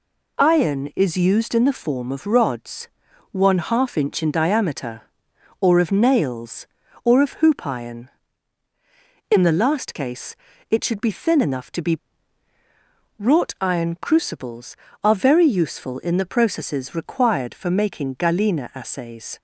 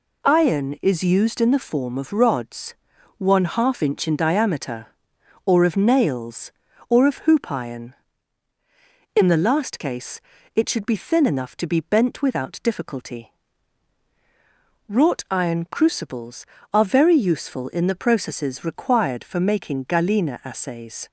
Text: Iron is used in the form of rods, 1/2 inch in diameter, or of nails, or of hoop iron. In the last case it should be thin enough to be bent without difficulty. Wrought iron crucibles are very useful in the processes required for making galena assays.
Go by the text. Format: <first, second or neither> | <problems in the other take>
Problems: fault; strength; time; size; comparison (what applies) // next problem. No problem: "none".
second | pauses between "case" and "it"; slight; at 10.3 s; 0.36 s long; slight in the second // skips "bent without difficulty"; at 12.5 s